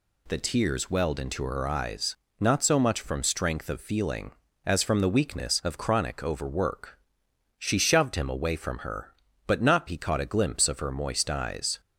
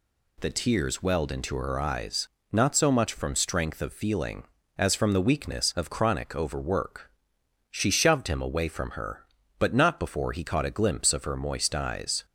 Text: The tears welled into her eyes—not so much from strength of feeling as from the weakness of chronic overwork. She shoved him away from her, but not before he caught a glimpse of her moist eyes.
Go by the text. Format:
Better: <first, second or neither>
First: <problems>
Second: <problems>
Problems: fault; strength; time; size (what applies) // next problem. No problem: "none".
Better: second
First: skips "before"; at 9.8 s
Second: none